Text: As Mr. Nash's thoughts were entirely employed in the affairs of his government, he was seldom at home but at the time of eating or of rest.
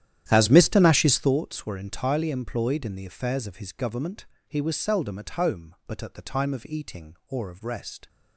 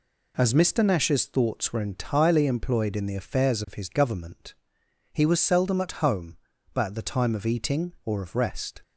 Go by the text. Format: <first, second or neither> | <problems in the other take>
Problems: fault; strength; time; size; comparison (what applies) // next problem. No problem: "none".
second | starts louder than the rest; strong; until 1.3 s; 11 dB